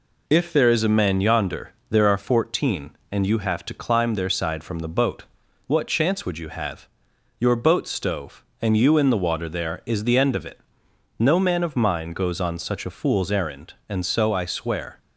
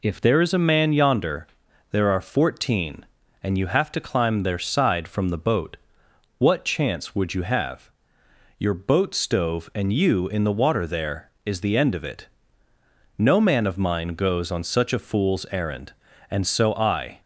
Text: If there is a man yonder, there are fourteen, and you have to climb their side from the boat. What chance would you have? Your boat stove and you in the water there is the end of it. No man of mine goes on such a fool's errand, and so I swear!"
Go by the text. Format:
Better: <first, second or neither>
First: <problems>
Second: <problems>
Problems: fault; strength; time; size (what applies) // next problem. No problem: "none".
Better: first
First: none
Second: stops before "swear"; at 17.2 s